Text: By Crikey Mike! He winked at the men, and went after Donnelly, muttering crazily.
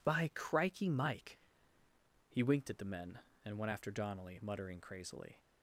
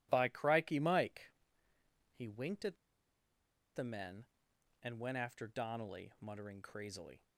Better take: first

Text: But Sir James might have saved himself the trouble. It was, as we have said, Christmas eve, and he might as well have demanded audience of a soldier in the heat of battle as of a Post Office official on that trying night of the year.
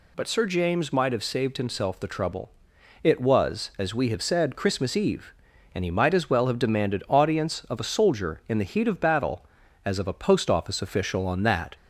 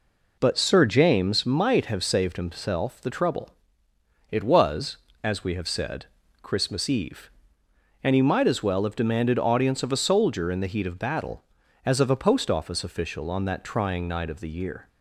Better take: second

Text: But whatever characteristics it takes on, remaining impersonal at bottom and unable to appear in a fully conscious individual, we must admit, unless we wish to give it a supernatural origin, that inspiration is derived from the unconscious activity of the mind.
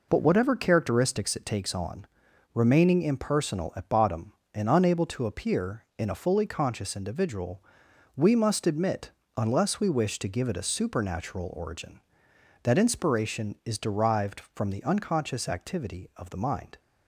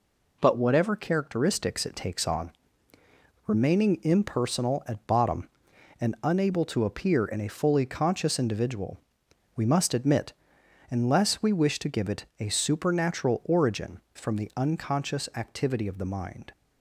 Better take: first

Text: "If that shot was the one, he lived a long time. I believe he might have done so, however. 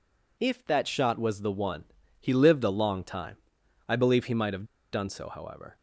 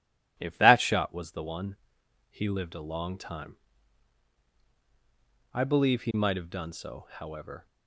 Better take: second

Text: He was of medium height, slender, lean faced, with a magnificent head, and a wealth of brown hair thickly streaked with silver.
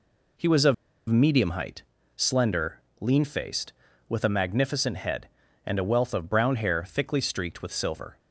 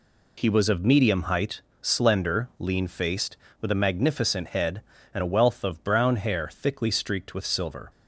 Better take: second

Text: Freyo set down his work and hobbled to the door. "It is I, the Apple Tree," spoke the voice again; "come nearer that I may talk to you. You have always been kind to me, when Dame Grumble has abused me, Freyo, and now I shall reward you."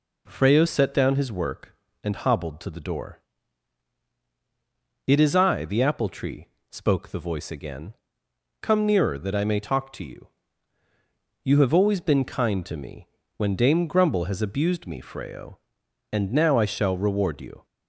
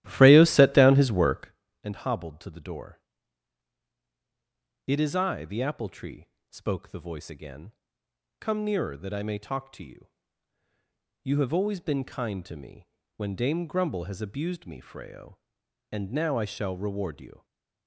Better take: first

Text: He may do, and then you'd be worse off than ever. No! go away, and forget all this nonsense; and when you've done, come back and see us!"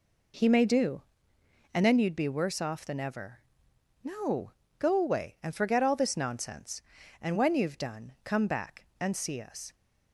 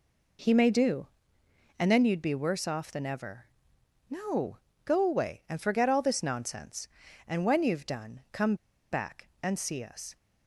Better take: first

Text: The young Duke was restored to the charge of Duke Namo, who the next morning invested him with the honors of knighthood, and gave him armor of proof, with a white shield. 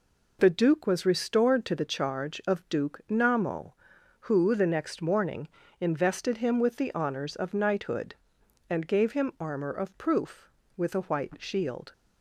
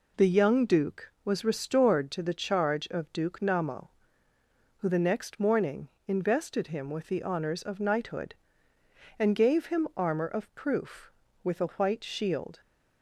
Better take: second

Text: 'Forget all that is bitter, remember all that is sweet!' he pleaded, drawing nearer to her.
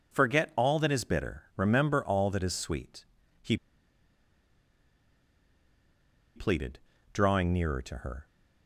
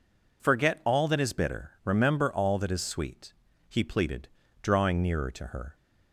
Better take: second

